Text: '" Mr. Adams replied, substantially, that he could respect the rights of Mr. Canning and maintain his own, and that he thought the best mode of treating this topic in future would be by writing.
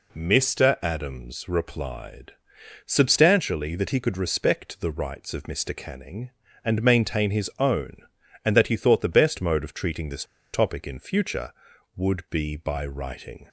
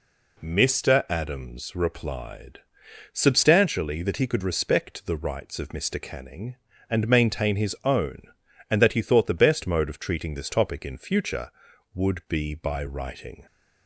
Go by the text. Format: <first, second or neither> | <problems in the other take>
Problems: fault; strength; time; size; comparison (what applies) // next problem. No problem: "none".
second | pauses between "this" and "topic"; slight; at 10.2 s; 0.28 s long